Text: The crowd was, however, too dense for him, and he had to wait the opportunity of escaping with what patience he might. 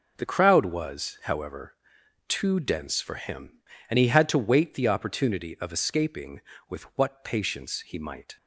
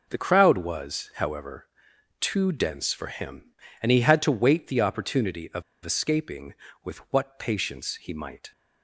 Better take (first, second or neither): first